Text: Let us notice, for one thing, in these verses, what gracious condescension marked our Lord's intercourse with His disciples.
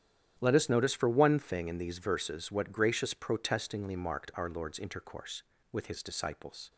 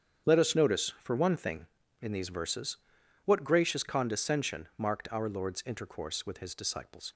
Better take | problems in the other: second | starts louder than the rest; strong; until 1.4 s; 10 dB; strong in the second // says "protestingly" for "condescension"; at 3.1 s

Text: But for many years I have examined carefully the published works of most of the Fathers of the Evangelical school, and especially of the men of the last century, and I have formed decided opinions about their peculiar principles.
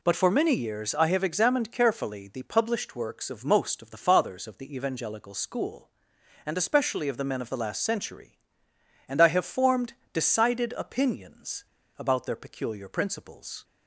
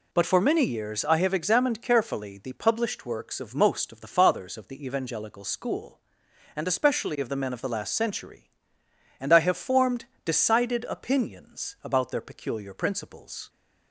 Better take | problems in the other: second | pauses between "formed" and "decided"; slight; at 9.9 s; 0.18 s long; slight in the second // pauses between "opinions" and "about"; slight; at 11.6 s; 0.32 s long

